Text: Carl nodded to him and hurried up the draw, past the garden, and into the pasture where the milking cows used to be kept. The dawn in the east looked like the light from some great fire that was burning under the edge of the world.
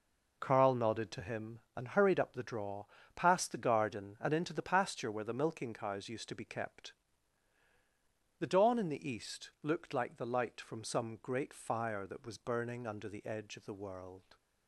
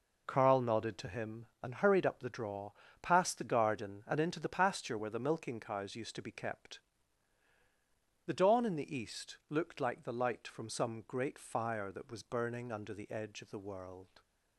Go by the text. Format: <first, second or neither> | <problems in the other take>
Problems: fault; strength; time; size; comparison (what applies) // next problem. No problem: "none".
neither | none